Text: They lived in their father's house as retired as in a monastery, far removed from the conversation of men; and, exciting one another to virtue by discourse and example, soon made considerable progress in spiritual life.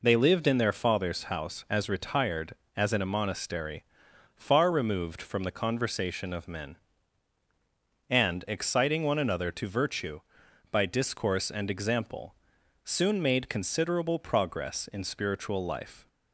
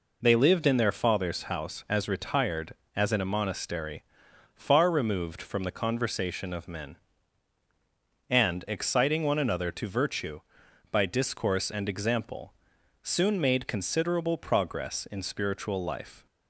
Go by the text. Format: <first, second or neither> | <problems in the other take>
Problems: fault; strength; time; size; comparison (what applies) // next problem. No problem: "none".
neither | none